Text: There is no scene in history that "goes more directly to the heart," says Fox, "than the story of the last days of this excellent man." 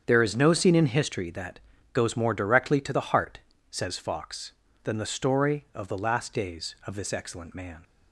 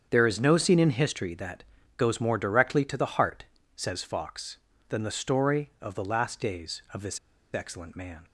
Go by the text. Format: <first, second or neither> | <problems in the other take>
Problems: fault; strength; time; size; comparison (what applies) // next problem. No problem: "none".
first | starts louder than the rest; strong; until 1.1 s; 7.5 dB; strong in the first // pauses between "that" and "goes"; slight; at 1.6 s; 0.32 s long; slight in the first // pauses between "this" and "excellent"; slight; at 7.1 s; 0.35 s long